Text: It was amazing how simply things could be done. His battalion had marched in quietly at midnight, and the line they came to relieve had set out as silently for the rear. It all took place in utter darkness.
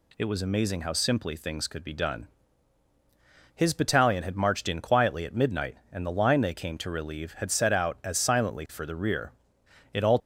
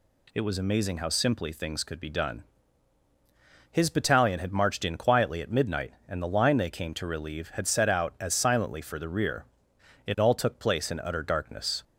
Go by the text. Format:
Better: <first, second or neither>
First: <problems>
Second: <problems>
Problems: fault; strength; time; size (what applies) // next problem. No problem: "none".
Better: second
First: stops before "took place in utter darkness"; at 10.2 s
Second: none